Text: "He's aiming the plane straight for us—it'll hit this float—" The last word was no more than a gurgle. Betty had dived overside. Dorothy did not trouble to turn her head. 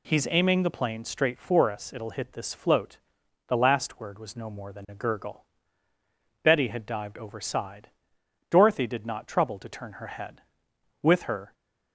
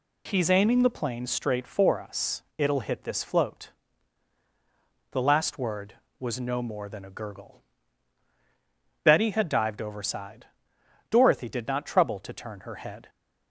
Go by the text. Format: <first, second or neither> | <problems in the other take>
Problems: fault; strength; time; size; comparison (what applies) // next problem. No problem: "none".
second | goes on to say "With her"; from 11.0 s on; 0.50 s long